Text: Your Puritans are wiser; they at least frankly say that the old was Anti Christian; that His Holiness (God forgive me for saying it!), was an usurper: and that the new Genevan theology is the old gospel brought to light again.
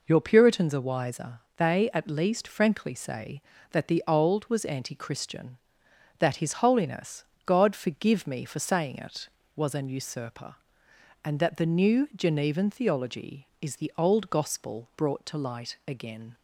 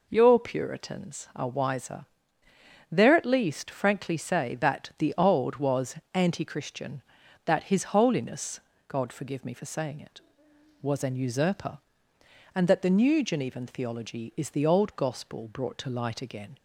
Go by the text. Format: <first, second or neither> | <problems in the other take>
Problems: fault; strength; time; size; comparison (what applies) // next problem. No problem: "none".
first | says "there" for "they"; at 2.9 s // pauses between "was" and "Anti"; slight; at 5.9 s; 0.18 s long